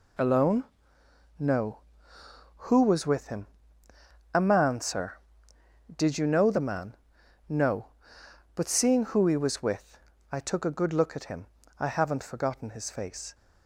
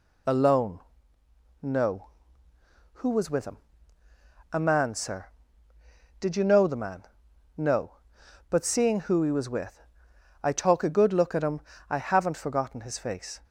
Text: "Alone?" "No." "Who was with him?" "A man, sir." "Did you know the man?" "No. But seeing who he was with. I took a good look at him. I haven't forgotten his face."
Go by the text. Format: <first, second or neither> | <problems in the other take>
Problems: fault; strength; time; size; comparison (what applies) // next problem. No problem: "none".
first | says "talk" for "took"; at 10.5 s